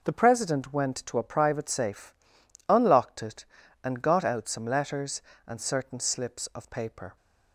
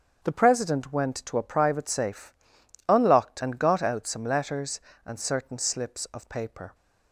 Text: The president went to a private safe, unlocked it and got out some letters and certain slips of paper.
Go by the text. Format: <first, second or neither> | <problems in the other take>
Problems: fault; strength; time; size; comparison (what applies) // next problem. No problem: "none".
first | starts louder than the rest; until 1.2 s; 7 dB // skips "it"; at 3.4 s